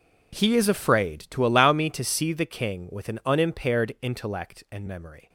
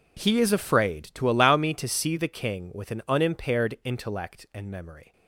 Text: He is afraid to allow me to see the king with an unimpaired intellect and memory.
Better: neither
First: none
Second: none

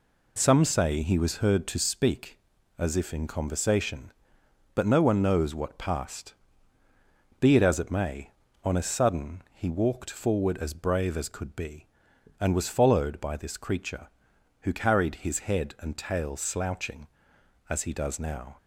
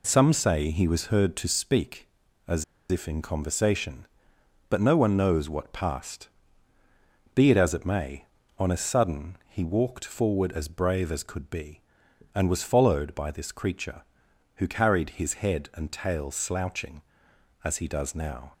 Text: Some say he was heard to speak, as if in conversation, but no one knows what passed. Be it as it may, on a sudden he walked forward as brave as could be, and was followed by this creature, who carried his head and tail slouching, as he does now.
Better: first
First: none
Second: pauses between "as" and "if"; slight; at 2.6 s; 0.26 s long

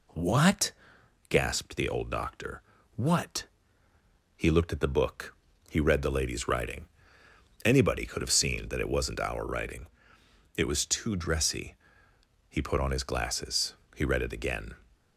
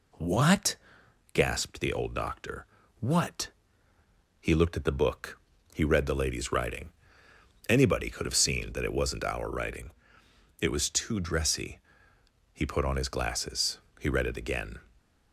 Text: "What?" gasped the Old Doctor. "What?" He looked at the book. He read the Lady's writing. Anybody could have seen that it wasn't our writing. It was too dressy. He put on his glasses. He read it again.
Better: neither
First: none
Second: none

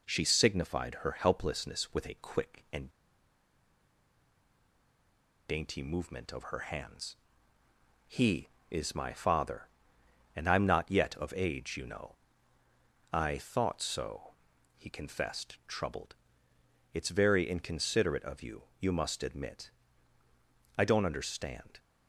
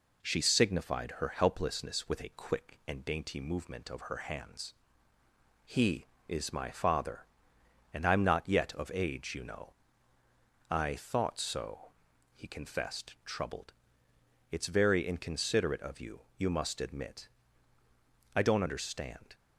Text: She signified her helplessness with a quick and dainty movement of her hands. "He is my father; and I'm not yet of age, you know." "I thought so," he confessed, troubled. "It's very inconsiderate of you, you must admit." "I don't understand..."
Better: second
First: pauses between "and" and "dainty"; strong; at 2.8 s; 2.5 s long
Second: none

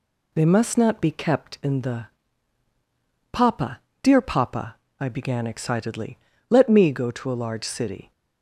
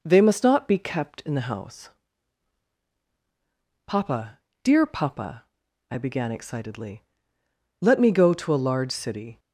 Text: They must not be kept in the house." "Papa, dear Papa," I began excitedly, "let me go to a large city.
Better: second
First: skips "house"; at 2.6 s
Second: none

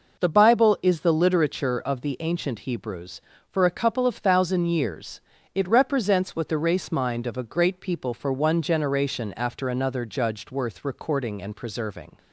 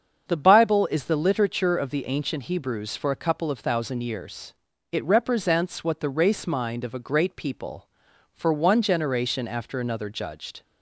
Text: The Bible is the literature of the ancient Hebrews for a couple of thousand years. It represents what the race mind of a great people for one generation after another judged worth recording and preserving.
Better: first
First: none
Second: starts louder than the rest; until 1.2 s; 7 dB // stops before "worth recording and preserving"; at 10.6 s

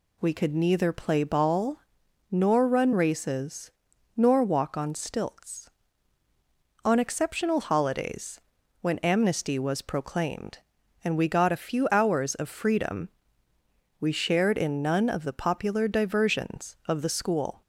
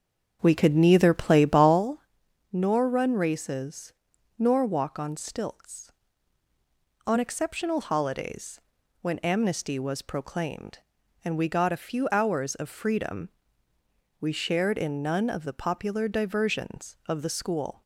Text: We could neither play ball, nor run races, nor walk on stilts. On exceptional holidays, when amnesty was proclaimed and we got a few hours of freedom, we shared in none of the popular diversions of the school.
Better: first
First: none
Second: starts louder than the rest; strong; until 1.8 s; 7.5 dB

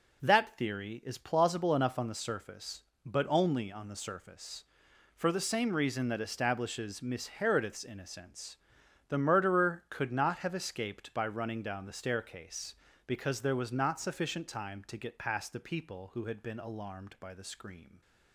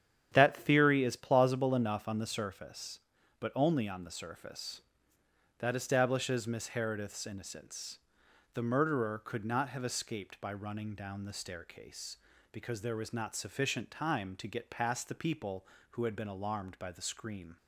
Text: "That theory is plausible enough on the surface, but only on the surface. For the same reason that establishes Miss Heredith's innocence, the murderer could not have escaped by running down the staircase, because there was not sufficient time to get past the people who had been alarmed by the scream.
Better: first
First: none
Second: starts louder than the rest; strong; until 1.3 s; 9 dB // skips "For the same reason"; at 5.1 s

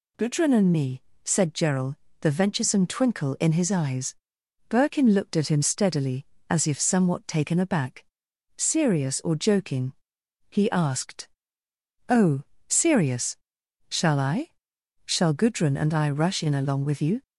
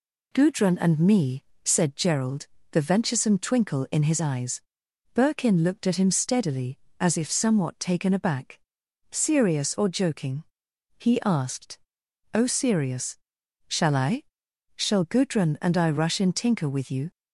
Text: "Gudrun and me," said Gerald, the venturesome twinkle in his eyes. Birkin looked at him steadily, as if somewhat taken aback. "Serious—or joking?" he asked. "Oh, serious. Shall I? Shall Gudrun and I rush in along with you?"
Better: first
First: none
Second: says "tinker" for "along"; at 16.3 s

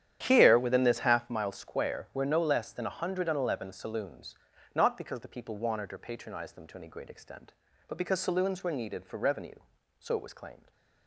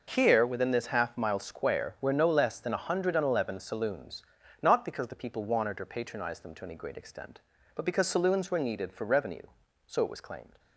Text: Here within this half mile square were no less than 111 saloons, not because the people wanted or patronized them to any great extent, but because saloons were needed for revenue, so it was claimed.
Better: second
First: starts louder than the rest; strong; until 1.4 s; 10.5 dB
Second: none

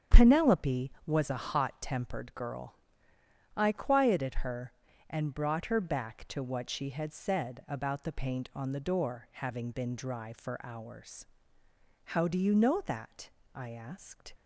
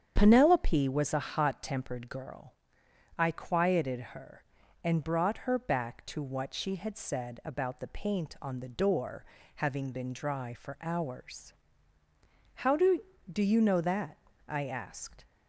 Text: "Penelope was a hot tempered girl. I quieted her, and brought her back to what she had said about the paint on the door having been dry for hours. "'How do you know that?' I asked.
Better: first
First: starts louder than the rest; until 1.2 s; 7 dB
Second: starts louder than the rest; strong; until 1.1 s; 8.5 dB // pauses between "door" and "having"; slight; at 9.2 s; 0.30 s long // says "do" twice; at 13.3 s

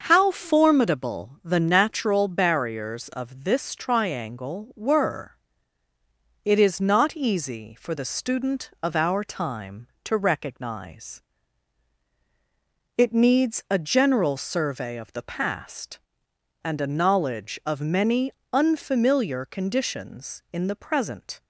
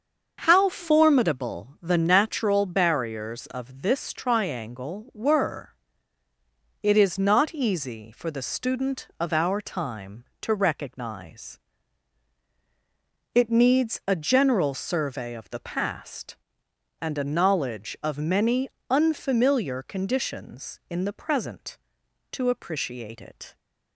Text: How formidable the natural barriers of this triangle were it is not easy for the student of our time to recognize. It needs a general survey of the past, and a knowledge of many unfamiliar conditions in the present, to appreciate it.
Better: second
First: starts louder than the rest; until 1.0 s; 6.5 dB // pauses between "were" and "it"; at 5.3 s; 1.0 s long // pauses between "many" and "unfamiliar"; slight; at 18.3 s; 0.22 s long // stops before "to appreciate it"; at 21.4 s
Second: starts louder than the rest; until 1.4 s; 6.5 dB // pauses between "were" and "it"; at 5.7 s; 1.0 s long // pauses between "many" and "unfamiliar"; slight; at 18.6 s; 0.22 s long

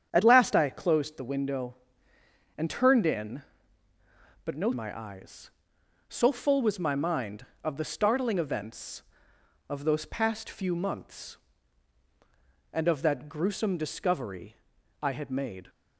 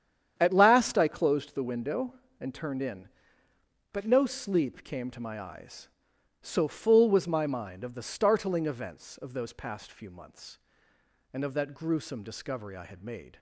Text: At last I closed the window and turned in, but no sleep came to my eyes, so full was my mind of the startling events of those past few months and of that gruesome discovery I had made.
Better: second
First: starts louder than the rest; strong; until 1.1 s; 8.5 dB // skips "sleep came to"; at 4.7 s // pauses between "discovery" and "I"; noticeable; at 14.5 s; 0.46 s long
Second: starts louder than the rest; strong; until 1.3 s; 9 dB

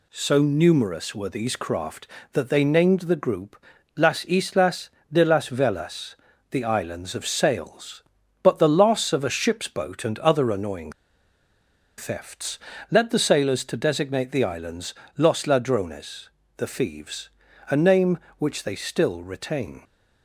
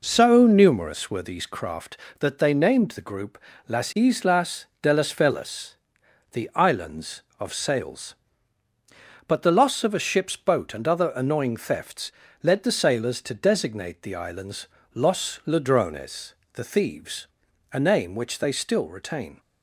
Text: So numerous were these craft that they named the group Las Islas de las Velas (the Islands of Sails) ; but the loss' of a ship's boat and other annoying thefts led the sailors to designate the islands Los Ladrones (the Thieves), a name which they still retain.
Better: second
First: pauses between "group" and "Las"; slight; at 3.6 s; 0.32 s long // pauses between "Islas" and "de"; slight; at 4.8 s; 0.24 s long // pauses between "annoying" and "thefts"; at 10.9 s; 1.0 s long // pauses between "thefts" and "led"; slight; at 12.5 s; 0.32 s long // pauses between "islands" and "Los"; slight; at 14.9 s; 0.20 s long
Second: pauses between "group" and "Las"; slight; at 3.3 s; 0.32 s long // pauses between "Islas" and "de"; slight; at 4.6 s; 0.16 s long // pauses between "thefts" and "led"; slight; at 12.1 s; 0.32 s long // pauses between "islands" and "Los"; slight; at 14.6 s; 0.26 s long

